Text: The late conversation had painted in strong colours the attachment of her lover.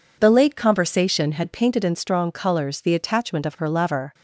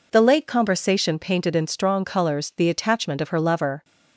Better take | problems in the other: first | skips "had"; at 1.1 s

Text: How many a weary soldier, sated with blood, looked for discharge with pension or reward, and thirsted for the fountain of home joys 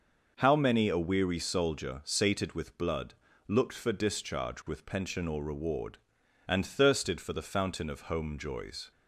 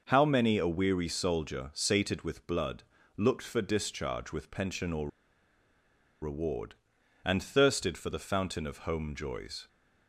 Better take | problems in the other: first | pauses between "or" and "reward"; at 5.0 s; 1.1 s long

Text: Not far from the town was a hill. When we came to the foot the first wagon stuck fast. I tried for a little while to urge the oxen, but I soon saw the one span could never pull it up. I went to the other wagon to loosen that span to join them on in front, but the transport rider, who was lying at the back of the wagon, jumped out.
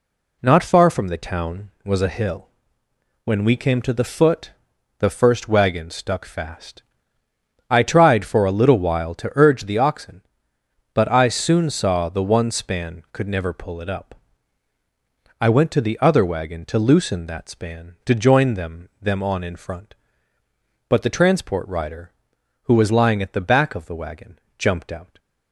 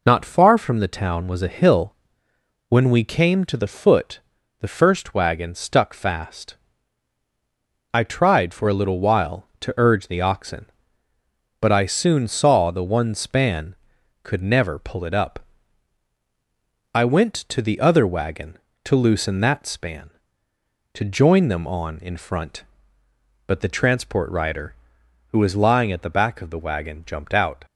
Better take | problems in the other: second | pauses between "foot" and "the"; noticeable; at 4.5 s; 0.46 s long; also in the second // says "them" twice; at 19.0 s

